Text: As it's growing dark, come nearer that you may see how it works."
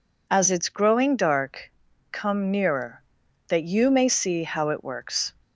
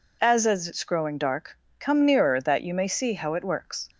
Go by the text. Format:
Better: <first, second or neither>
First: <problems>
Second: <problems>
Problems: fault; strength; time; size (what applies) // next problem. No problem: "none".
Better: first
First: none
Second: says "As" twice; at 0.4 s